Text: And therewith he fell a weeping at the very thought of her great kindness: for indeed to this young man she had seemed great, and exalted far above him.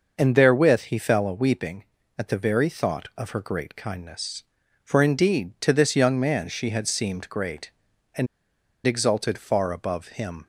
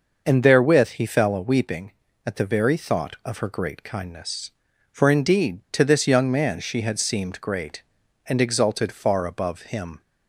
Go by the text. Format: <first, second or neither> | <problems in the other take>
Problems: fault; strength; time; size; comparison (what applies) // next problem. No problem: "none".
second | pauses between "and" and "exalted"; noticeable; at 8.2 s; 0.59 s long